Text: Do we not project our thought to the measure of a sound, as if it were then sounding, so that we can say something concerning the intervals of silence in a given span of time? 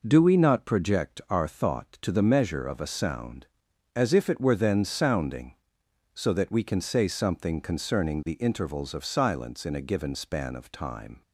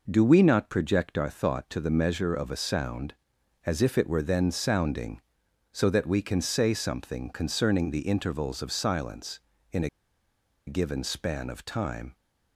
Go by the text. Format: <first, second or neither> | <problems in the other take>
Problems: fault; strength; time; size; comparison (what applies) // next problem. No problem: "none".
first | pauses between "a" and "given"; noticeable; at 9.8 s; 0.78 s long